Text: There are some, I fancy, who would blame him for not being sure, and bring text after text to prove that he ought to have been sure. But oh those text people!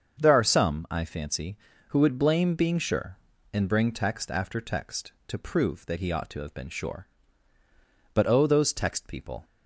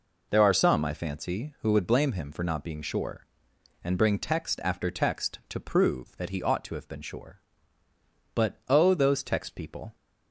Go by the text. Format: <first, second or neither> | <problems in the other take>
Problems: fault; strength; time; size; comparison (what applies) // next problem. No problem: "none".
second | starts louder than the rest; until 1.2 s; 7 dB // skips "him for not"; at 2.5 s